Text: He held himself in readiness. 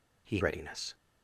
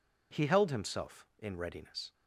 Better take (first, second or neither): second